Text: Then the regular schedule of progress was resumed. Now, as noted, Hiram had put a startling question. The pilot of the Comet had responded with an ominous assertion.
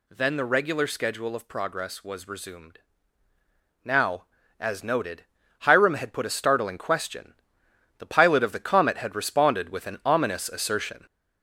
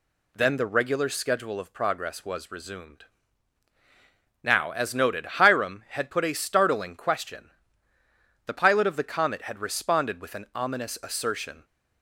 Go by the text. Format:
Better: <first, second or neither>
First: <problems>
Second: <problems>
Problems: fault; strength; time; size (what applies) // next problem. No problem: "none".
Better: second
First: gets louder; noticeable; throughout; 5 dB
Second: none